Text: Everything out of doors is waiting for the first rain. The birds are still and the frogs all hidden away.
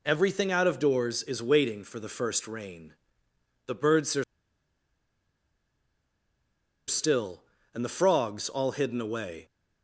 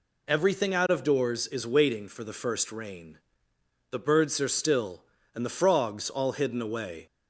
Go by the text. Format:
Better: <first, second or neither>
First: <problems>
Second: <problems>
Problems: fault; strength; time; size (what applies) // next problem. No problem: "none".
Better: second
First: pauses between "are" and "still"; strong; at 4.2 s; 2.6 s long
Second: none